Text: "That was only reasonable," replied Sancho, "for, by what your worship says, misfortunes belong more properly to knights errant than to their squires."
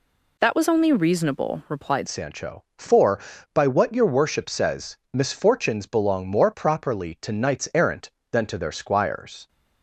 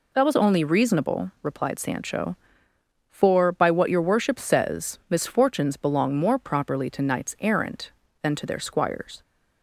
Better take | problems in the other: second | changes voice at "Sancho"; from 2.0 s on; 7.4 s long

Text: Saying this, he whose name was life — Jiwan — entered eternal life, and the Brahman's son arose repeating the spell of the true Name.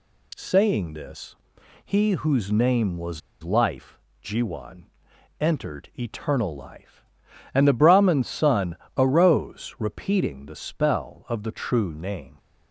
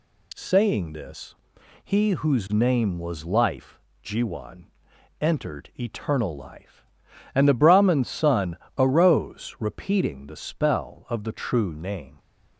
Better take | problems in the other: second | pauses between "was" and "life"; slight; at 3.2 s; 0.21 s long // pauses between "son" and "arose"; slight; at 8.7 s; 0.20 s long; slight in the second

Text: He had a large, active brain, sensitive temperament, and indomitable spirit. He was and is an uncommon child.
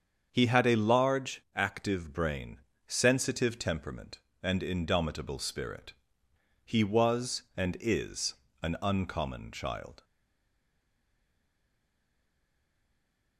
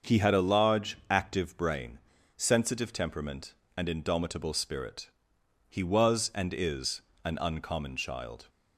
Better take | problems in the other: second | starts louder than the rest; strong; until 1.3 s; 7 dB; also in the second // pauses between "is" and "an"; slight; at 8.3 s; 0.28 s long; slight in the second // stays silent after the last word; strong; from 10.0 s on; 3.3 s long

